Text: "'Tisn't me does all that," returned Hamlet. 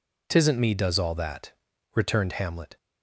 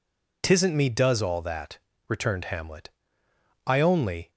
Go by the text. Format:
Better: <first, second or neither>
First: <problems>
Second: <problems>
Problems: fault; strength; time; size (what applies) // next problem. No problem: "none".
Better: first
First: none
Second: goes on to say "I only"; noticeable; from 3.6 s on; 0.64 s long